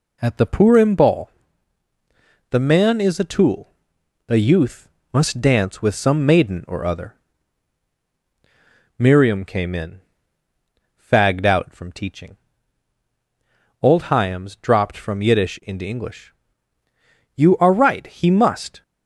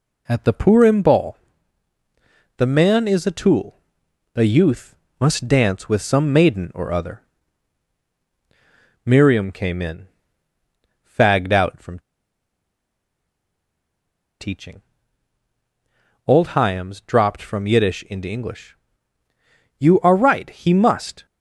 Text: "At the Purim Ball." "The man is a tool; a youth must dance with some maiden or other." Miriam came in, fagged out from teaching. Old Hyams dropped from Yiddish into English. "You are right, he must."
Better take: first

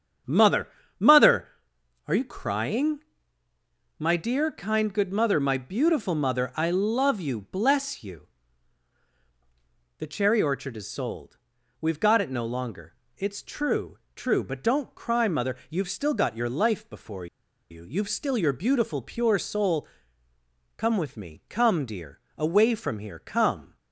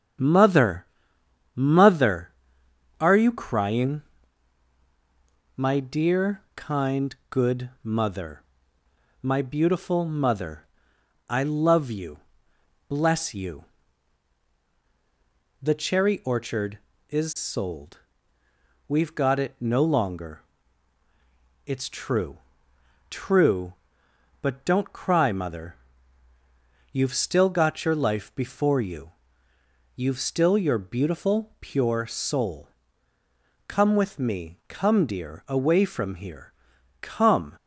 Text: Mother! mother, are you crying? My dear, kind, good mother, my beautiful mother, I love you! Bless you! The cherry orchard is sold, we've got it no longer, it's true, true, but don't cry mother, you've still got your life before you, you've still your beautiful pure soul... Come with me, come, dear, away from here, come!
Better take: second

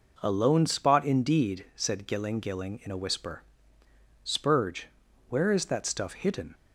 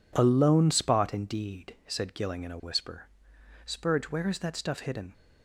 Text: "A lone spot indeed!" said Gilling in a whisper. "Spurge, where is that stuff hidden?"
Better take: second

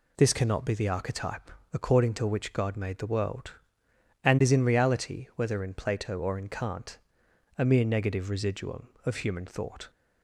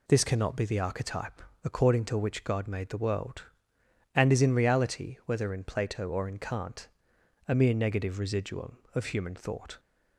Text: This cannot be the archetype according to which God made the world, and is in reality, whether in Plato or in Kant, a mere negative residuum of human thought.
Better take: neither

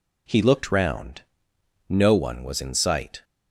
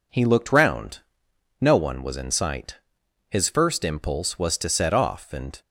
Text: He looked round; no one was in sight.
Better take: first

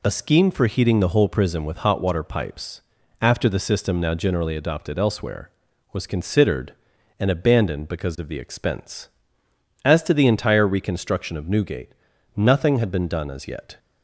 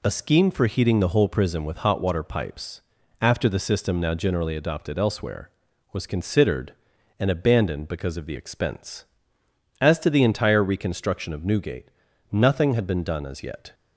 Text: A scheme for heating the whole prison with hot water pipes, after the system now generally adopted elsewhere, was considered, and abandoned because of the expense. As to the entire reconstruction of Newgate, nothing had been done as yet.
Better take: neither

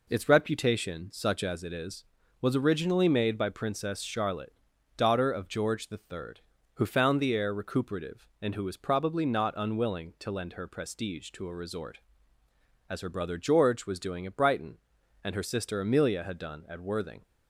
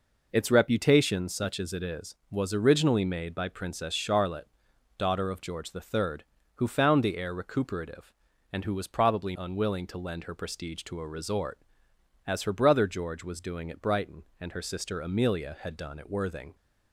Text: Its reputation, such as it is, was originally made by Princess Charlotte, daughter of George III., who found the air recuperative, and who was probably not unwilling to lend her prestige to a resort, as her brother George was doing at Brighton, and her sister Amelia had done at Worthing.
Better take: first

